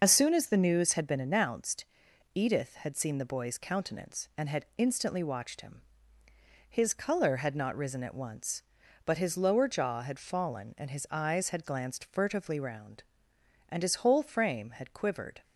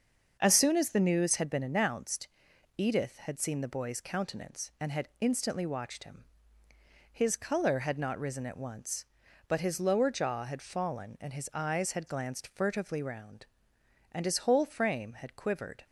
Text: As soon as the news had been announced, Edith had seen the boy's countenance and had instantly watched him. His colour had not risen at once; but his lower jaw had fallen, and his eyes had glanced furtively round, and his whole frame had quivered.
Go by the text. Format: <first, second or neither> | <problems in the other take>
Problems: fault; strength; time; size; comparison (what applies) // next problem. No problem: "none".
second | loses the start of "As"; at 0.0 s; 55 ms // starts louder than the rest; noticeable; until 1.0 s; 6 dB; also in the second